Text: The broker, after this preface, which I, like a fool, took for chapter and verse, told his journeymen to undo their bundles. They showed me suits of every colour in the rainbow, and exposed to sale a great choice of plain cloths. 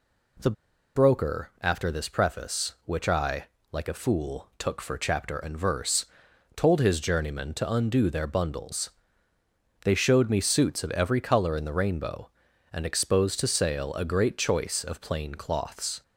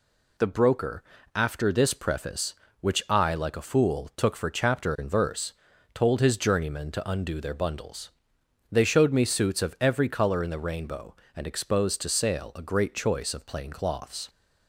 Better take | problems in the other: second | pauses between "The" and "broker"; at 0.4 s; 0.45 s long

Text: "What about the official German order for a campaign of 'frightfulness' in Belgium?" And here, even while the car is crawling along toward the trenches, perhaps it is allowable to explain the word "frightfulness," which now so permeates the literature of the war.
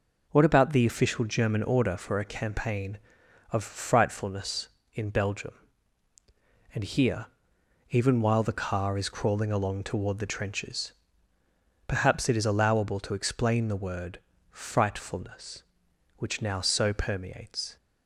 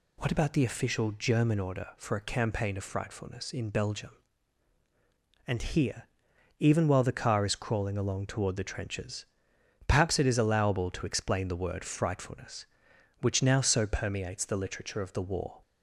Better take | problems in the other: second | pauses between "word" and "frightfulness"; slight; at 14.1 s; 0.30 s long // stops before "the literature of the war"; at 17.7 s

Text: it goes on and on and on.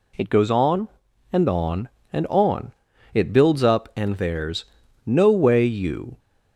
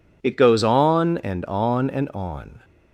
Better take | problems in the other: second | goes on to say "It builds up and there's no way you"; strong; from 3.1 s on; 3.0 s long

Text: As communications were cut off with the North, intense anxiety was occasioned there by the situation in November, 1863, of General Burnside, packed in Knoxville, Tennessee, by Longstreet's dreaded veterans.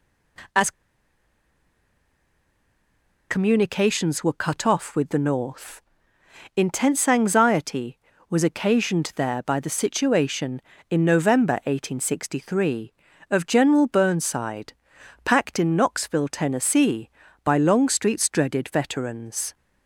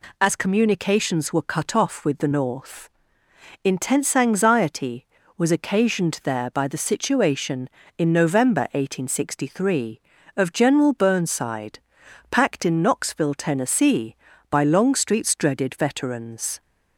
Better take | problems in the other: second | pauses between "As" and "communications"; strong; at 0.7 s; 2.5 s long

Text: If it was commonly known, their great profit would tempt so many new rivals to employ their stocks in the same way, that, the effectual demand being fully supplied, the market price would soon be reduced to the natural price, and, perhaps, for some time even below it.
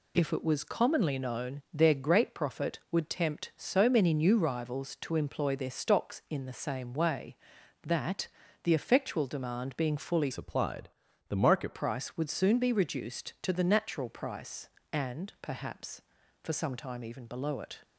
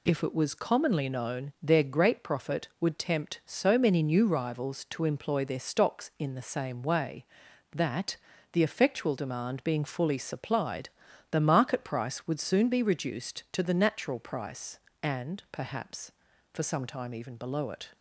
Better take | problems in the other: second | changes voice from "supplied" to "market"; from 10.3 to 11.7 s; 1.4 s long

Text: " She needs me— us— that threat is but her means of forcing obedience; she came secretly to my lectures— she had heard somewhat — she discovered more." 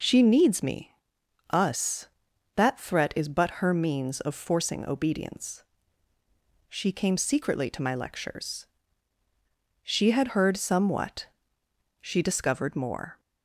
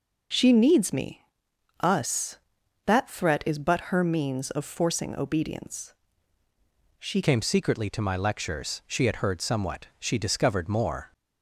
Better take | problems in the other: first | changes voice at "came"; from 7.2 s on; 3.9 s long

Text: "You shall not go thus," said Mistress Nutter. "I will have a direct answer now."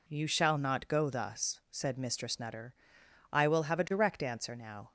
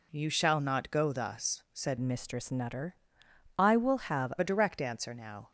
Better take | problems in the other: first | changes voice from "Mistress" to "have"; from 1.9 to 4.3 s; 2.4 s long

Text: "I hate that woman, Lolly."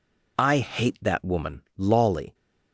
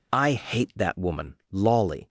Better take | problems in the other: neither | none

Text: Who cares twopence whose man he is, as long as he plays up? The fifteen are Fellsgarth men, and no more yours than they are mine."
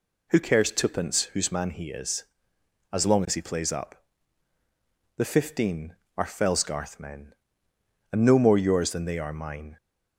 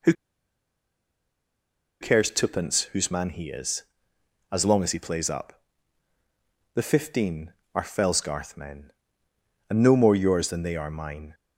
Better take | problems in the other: first | pauses between "Who" and "cares"; strong; at 0.1 s; 1.8 s long

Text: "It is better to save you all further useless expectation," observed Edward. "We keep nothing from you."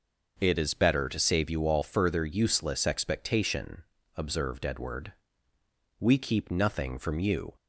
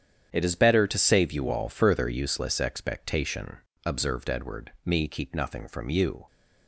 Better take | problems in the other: first | starts louder than the rest; strong; until 1.3 s; 9 dB // says "Me" for "We"; at 4.8 s

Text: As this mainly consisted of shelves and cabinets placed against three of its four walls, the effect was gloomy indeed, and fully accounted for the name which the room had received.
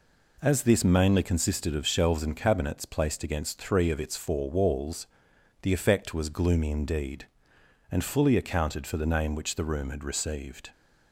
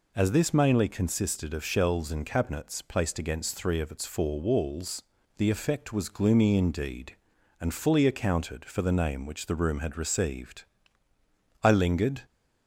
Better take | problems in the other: first | goes on to say "I lingered"; from 11.6 s on; 0.60 s long

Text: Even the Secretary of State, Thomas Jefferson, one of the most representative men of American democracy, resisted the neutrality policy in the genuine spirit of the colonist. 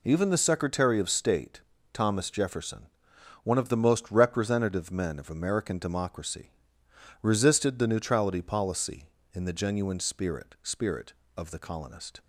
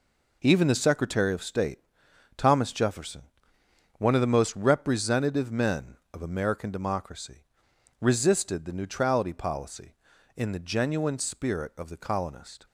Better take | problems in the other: second | says "spirit" twice; at 10.6 s

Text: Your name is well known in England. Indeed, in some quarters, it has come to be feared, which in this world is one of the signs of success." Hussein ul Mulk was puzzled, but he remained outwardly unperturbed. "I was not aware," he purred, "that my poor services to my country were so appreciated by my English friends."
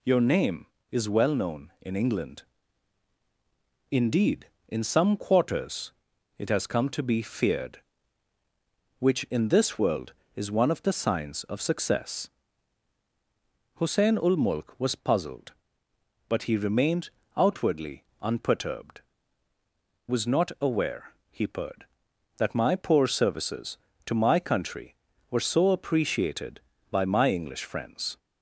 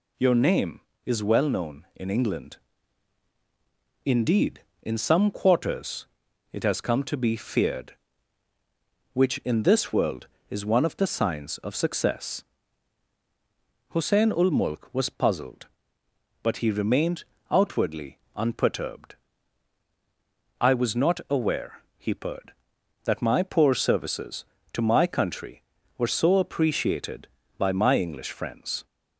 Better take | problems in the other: second | pauses between "remained" and "outwardly"; slight; at 17.1 s; 0.26 s long; slight in the second // pauses between "outwardly" and "unperturbed"; slight; at 18.0 s; 0.18 s long; slight in the second // skips "I"; at 19.5 s

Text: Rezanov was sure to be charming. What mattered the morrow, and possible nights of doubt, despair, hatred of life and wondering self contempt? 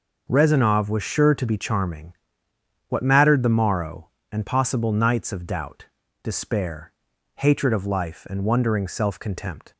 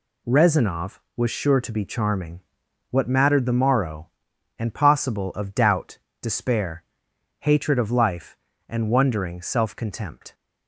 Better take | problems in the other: first | skips "nights"; at 5.3 s

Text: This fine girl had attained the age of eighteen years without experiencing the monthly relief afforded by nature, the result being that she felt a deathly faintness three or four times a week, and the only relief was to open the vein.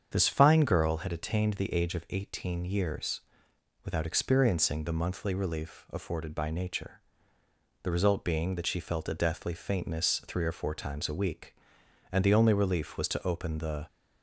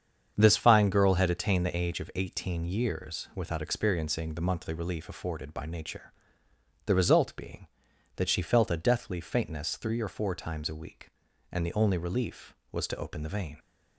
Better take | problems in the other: second | starts louder than the rest; strong; until 1.1 s; 7.5 dB; strong in the second // pauses between "years" and "without"; noticeable; at 3.2 s; 0.62 s long // stops before "vein"; at 13.8 s

